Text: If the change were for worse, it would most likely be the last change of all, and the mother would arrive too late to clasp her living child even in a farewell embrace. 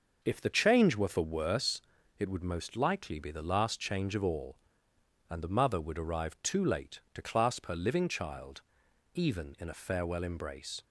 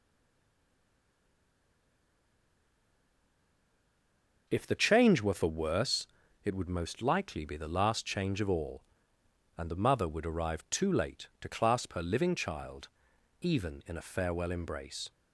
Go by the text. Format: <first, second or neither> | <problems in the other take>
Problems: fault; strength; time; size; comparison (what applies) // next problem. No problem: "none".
first | stays silent before the first word; strong; until 4.4 s; 4.4 s long // pauses between "child" and "even"; noticeable; at 12.8 s; 0.54 s long; noticeable in the first